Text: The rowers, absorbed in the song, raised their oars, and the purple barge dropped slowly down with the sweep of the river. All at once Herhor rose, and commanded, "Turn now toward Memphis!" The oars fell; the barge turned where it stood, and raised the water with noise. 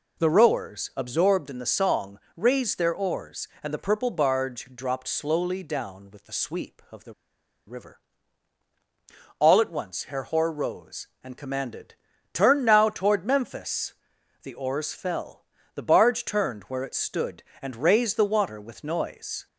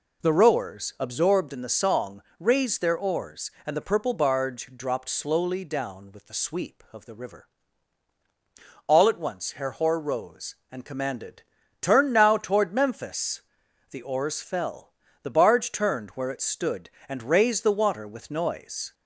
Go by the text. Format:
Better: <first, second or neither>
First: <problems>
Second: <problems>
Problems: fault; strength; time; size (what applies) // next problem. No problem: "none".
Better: second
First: pauses between "the" and "river"; noticeable; at 7.1 s; 0.53 s long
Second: none